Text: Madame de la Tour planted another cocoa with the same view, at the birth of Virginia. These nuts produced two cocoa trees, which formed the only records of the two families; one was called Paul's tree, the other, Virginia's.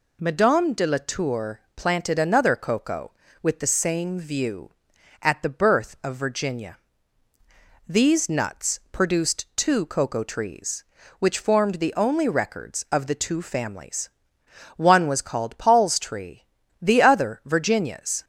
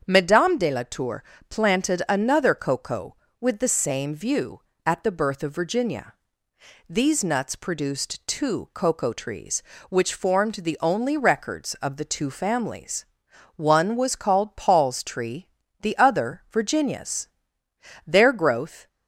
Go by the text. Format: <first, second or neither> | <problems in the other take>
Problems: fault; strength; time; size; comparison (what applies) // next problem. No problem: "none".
first | starts louder than the rest; strong; until 1.0 s; 7.5 dB // pauses between "Tour" and "planted"; slight; at 1.2 s; 0.26 s long // goes on to say "Their growth"; noticeable; from 18.0 s on; 0.80 s long